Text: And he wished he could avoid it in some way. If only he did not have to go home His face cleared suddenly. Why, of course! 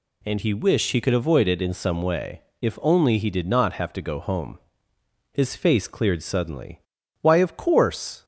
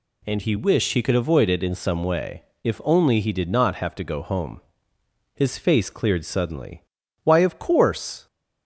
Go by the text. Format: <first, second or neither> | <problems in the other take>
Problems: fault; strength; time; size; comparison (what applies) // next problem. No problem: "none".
neither | pauses between "home" and "His"; noticeable; the same in both